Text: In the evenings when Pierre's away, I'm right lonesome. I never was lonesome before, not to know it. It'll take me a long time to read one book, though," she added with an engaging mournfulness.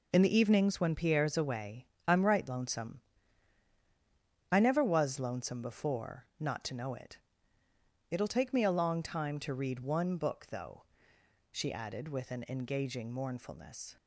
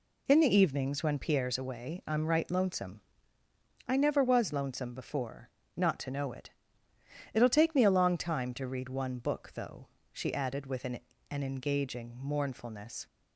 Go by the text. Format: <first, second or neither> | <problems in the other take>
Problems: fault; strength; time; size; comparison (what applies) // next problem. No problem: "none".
first | says "an" twice; at 11.3 s